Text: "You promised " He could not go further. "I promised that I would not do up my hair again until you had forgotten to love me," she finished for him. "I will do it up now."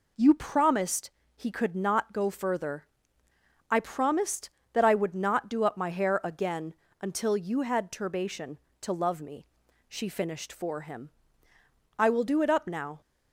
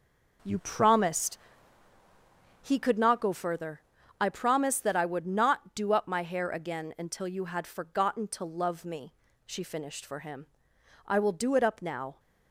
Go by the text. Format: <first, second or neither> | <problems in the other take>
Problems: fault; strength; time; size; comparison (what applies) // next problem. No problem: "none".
second | pauses between "again" and "until"; slight; at 6.7 s; 0.26 s long // says "turbation" for "forgotten"; at 7.9 s